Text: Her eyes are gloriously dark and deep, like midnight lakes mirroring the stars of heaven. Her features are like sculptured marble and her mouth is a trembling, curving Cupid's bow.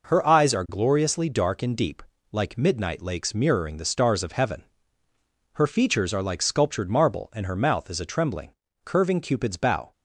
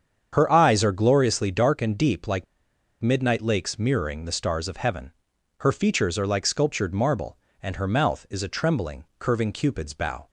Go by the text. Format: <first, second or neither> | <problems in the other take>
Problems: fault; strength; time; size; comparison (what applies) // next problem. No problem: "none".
first | starts louder than the rest; strong; until 1.3 s; 7.5 dB // pauses between "like" and "midnight"; noticeable; at 2.4 s; 0.58 s long